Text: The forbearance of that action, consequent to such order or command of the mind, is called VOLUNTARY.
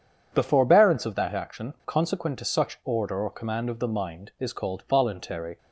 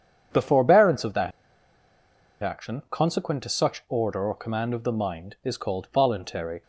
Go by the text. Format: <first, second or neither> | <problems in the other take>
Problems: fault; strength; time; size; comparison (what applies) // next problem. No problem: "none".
first | pauses between "that" and "action"; at 1.3 s; 1.1 s long